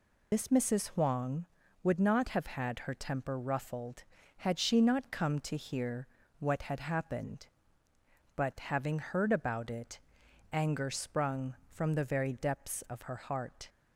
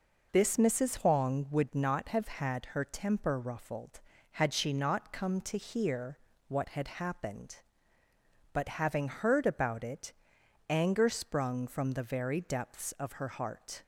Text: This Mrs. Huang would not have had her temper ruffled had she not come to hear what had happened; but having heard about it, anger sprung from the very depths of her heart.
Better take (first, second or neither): second